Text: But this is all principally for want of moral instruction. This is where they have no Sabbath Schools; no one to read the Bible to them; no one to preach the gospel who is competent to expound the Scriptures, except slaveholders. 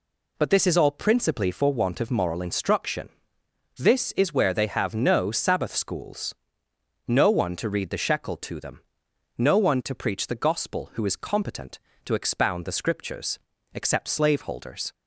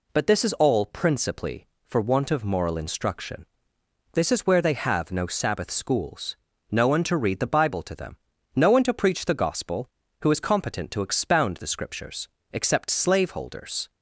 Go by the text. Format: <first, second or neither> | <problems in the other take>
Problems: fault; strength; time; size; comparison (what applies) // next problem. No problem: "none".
second | says "Shekel" for "Bible"; at 8.0 s